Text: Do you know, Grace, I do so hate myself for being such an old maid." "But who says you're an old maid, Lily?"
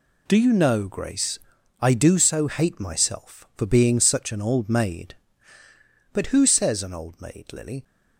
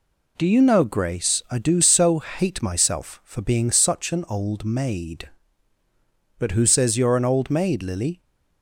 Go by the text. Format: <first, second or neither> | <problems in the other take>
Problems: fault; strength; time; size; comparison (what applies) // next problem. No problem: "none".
second | skips "you're"; at 6.8 s